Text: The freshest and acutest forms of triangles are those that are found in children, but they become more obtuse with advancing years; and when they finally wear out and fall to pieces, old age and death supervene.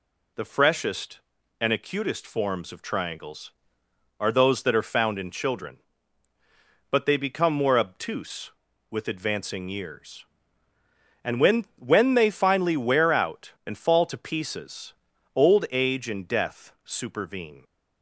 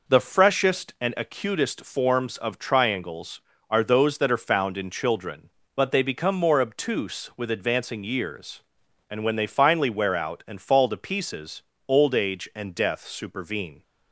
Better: second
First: says "when" twice; at 11.7 s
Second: none

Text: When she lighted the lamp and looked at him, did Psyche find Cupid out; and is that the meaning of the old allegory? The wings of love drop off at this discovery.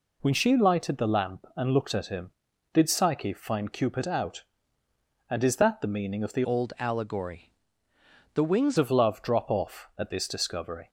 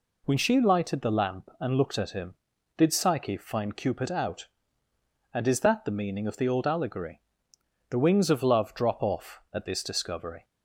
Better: second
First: changes voice from "old" to "wings"; from 6.4 to 8.7 s; 2.3 s long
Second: none

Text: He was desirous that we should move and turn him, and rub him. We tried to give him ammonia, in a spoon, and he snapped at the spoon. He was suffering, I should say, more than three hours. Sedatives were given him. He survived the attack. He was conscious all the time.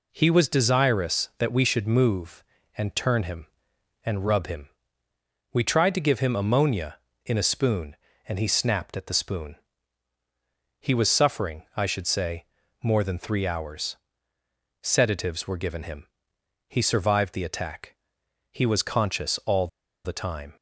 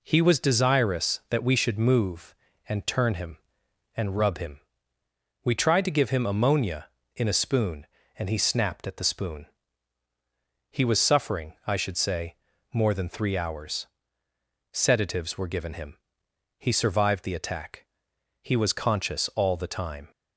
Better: second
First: pauses between "all" and "the"; at 19.6 s; 0.38 s long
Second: none

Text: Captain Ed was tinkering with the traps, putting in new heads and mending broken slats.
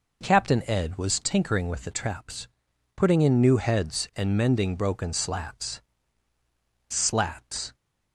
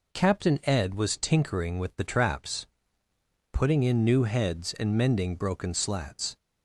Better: second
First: says "slats" twice; at 6.8 s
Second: none

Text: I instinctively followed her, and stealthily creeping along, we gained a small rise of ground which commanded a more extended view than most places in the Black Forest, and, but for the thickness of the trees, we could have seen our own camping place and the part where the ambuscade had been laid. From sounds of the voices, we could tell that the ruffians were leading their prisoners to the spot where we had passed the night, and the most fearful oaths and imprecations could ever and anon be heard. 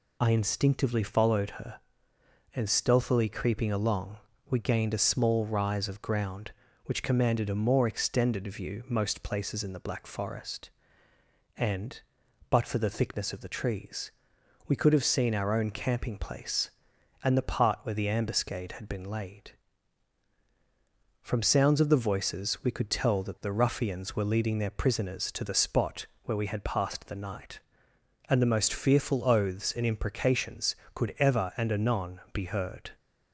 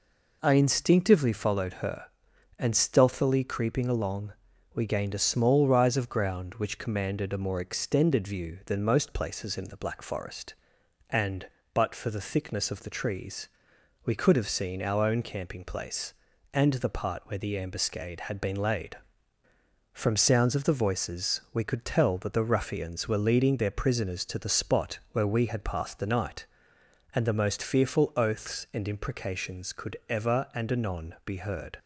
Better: second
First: skips "than"; at 8.8 s // pauses between "spot" and "where"; slight; at 26.0 s; 0.18 s long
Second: none

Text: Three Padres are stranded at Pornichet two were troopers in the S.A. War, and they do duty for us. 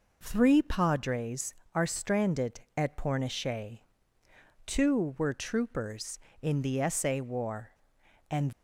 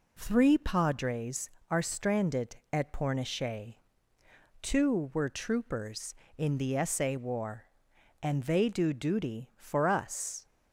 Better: second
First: pauses between "Pornichet" and "two"; noticeable; at 3.7 s; 0.86 s long // stops before "they do duty for us"; at 8.5 s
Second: pauses between "Pornichet" and "two"; noticeable; at 3.7 s; 0.86 s long

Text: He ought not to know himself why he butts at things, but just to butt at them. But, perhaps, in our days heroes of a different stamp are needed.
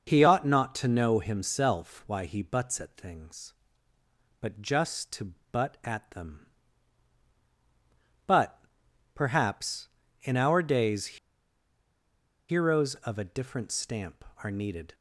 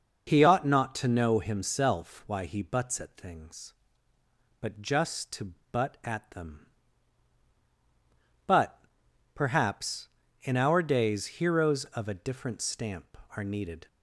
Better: second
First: pauses between "to" and "butt"; slight; at 5.3 s; 0.18 s long // pauses between "days" and "heroes"; strong; at 11.1 s; 1.3 s long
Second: pauses between "to" and "butt"; slight; at 5.5 s; 0.18 s long

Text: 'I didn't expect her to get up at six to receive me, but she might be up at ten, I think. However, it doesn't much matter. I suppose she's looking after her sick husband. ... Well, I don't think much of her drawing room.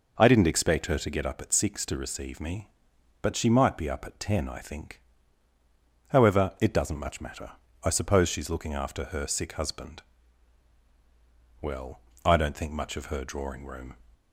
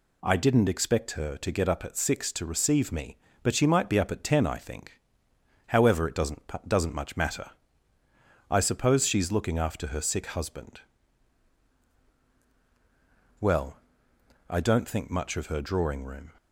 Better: first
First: none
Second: says "doesn't" twice; at 6.6 s

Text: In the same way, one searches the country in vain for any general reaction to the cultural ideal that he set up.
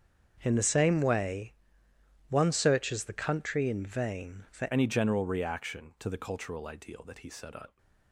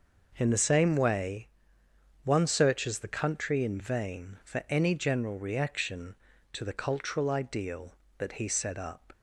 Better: second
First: starts louder than the rest; strong; until 1.4 s; 7.5 dB // changes voice at "any"; from 4.7 s on; 3.0 s long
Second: none

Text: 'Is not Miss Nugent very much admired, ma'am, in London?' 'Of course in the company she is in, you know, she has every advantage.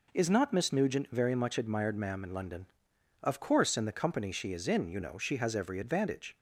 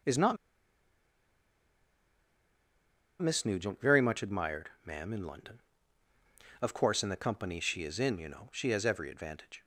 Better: first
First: none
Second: pauses between "not" and "Miss"; strong; at 0.3 s; 2.8 s long

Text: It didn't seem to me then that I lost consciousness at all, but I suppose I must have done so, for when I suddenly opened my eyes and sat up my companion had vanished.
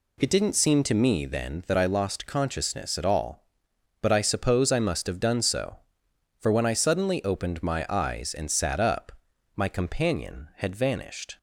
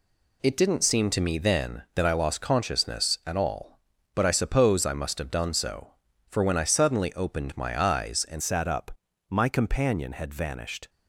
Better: first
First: pauses between "up" and "my"; noticeable; at 9.1 s; 0.48 s long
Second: changes voice at "sat"; from 8.4 s on; 2.4 s long // pauses between "up" and "my"; at 8.9 s; 0.42 s long

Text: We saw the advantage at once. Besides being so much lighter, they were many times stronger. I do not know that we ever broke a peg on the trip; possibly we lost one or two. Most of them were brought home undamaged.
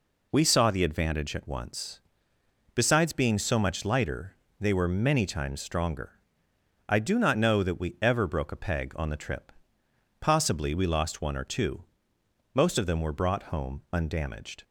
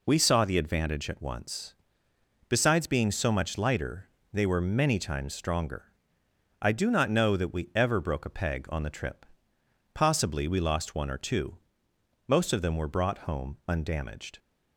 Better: neither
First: none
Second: none

